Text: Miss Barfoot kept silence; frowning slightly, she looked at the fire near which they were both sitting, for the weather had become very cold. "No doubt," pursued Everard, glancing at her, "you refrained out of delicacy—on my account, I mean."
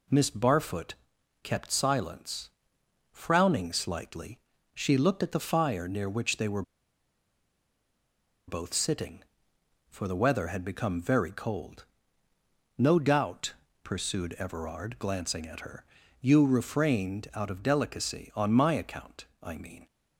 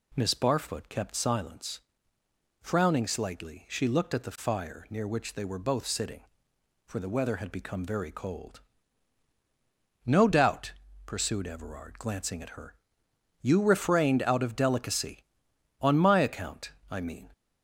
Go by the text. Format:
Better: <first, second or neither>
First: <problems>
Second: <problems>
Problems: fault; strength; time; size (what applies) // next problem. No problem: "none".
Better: second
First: pauses between "Barfoot" and "kept"; noticeable; at 0.9 s; 0.48 s long // pauses between "were" and "both"; strong; at 6.6 s; 1.8 s long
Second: none